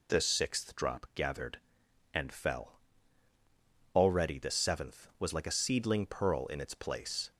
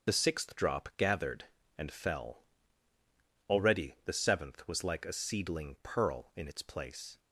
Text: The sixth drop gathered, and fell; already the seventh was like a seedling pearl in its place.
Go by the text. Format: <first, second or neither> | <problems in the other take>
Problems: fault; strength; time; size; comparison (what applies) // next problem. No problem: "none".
first | loses the start of "The"; at 0.0 s; 45 ms // starts louder than the rest; until 1.1 s; 6.5 dB